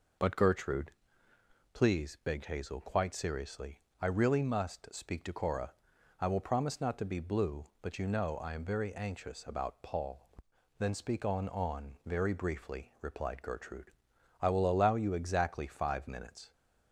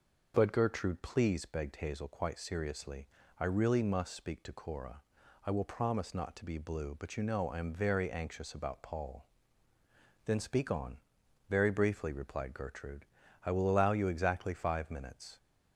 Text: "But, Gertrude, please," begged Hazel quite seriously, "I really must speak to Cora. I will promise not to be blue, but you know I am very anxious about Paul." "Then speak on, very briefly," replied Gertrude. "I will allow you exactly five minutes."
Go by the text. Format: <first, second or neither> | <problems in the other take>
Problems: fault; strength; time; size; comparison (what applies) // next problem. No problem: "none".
second | says "on" twice; at 11.4 s